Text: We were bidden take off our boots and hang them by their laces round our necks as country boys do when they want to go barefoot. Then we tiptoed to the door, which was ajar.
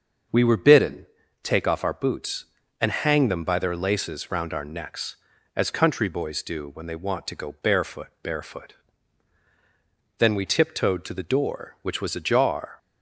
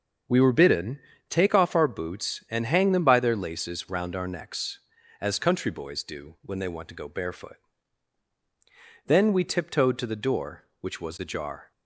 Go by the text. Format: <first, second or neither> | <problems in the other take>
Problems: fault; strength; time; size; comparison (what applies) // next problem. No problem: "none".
second | starts louder than the rest; until 1.6 s; 6 dB; also in the second // pauses between "bidden" and "take"; slight; at 1.0 s; 0.36 s long; slight in the second // says "barefoot" twice; at 8.2 s